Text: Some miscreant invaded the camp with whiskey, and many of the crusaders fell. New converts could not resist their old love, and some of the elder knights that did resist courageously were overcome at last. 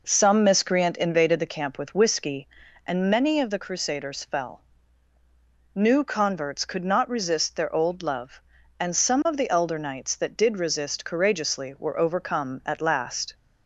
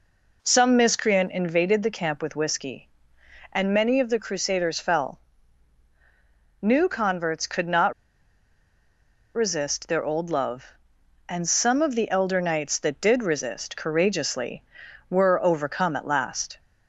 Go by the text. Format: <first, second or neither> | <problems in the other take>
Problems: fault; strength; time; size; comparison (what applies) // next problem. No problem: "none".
first | pauses between "not" and "resist"; strong; at 7.9 s; 1.4 s long